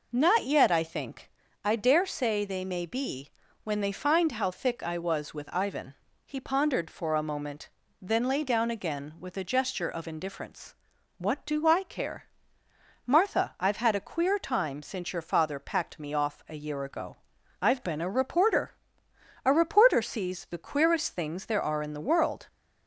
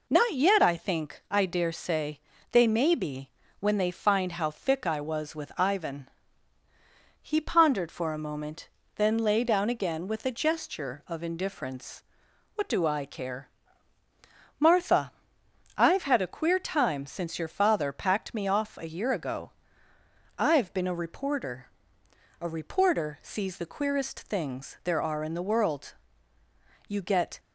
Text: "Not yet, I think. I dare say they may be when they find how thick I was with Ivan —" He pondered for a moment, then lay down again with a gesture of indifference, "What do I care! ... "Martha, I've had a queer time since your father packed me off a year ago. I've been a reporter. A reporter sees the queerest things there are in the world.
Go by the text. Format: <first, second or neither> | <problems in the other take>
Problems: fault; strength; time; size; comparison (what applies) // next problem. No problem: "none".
first | pauses between "say" and "they"; slight; at 2.1 s; 0.32 s long // pauses between "be" and "when"; slight; at 3.2 s; 0.30 s long; slight in the first // goes on to say "You get"; from 26.8 s on; 0.52 s long